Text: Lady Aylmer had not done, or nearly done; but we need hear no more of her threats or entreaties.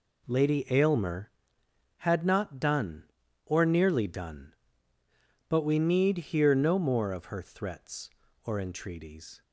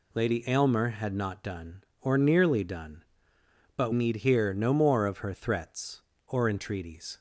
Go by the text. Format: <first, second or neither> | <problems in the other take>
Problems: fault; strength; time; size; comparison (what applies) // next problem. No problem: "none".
first | skips "we"; at 3.9 s